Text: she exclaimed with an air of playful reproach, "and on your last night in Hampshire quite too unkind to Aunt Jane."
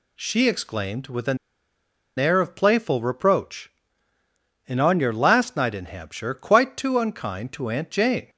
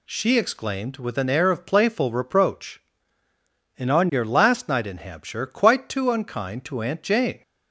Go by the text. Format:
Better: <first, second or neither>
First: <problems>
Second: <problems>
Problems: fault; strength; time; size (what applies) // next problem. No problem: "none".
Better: second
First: pauses between "an" and "air"; noticeable; at 1.3 s; 0.80 s long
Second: none